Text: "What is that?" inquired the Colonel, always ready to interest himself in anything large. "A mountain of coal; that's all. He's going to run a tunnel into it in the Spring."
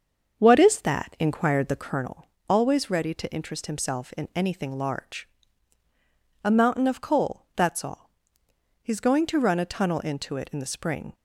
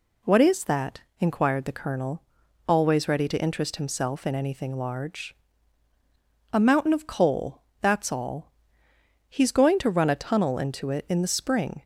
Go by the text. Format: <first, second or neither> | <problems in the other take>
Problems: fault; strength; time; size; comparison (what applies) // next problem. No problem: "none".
second | starts louder than the rest; until 2.1 s; 6.5 dB